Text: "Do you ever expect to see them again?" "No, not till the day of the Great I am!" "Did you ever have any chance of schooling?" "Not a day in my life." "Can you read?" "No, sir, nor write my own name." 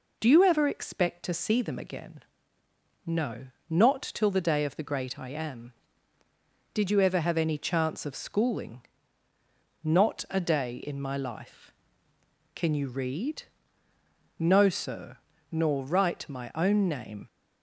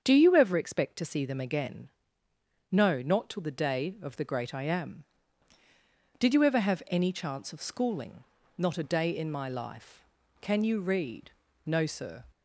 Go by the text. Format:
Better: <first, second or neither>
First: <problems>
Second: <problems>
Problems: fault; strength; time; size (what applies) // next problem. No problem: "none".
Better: first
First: none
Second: starts louder than the rest; strong; until 1.0 s; 7.5 dB // stops before "nor write my own name"; at 12.3 s